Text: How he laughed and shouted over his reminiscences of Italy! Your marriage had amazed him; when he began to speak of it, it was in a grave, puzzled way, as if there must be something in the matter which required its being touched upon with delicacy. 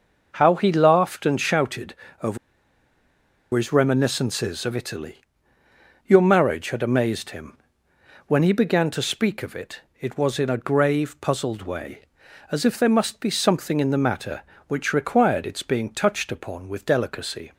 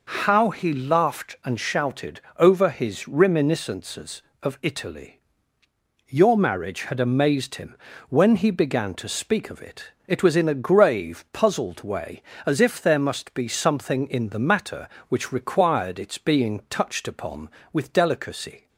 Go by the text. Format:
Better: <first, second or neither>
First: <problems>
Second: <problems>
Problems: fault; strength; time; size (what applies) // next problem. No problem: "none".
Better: second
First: pauses between "shouted" and "over"; slight; at 1.9 s; 0.30 s long // pauses between "over" and "his"; at 2.3 s; 1.1 s long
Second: pauses between "shouted" and "over"; slight; at 2.2 s; 0.16 s long